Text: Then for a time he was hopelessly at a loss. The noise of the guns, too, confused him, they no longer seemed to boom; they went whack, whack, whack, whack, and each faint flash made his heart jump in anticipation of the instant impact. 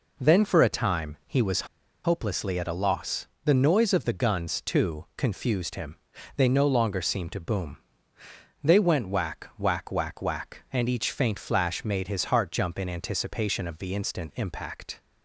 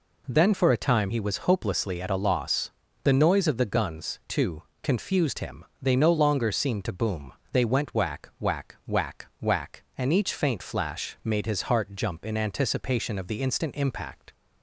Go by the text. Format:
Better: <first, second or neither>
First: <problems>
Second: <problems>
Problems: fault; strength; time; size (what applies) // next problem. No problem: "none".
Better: second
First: pauses between "was" and "hopelessly"; at 1.6 s; 0.37 s long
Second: none